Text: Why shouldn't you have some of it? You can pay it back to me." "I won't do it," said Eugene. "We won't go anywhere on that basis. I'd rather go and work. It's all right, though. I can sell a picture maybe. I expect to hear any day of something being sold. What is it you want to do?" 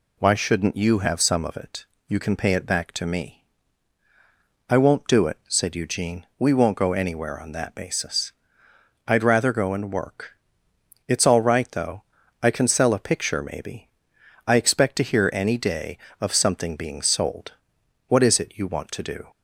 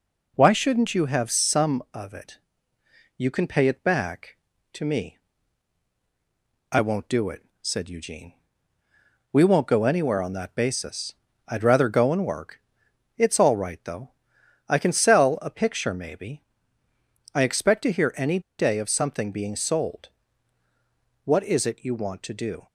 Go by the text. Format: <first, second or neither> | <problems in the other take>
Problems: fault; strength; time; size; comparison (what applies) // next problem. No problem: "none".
first | pauses between "any" and "day"; slight; at 18.4 s; 0.18 s long